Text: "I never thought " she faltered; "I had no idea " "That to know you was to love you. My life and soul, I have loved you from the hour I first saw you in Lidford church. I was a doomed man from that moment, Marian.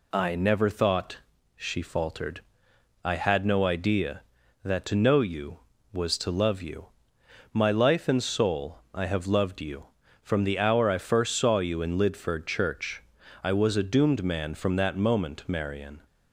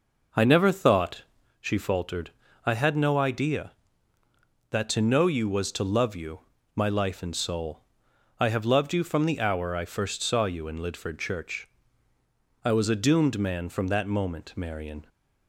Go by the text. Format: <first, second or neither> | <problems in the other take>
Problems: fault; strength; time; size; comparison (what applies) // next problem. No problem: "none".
first | starts louder than the rest; noticeable; until 1.5 s; 5.5 dB